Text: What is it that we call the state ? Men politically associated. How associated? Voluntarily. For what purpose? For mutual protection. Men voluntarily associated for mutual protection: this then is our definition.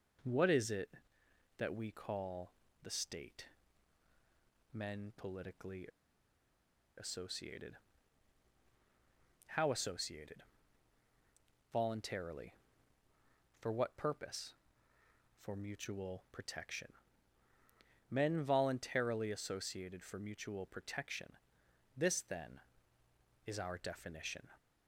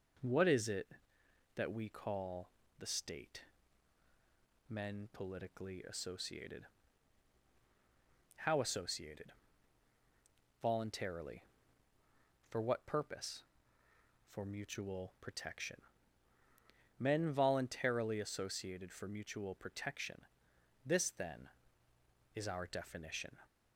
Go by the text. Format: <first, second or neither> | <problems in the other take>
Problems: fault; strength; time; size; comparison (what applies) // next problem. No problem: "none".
second | pauses between "call" and "the"; slight; at 2.5 s; 0.32 s long; slight in the second // pauses between "politically" and "associated"; at 5.8 s; 1.1 s long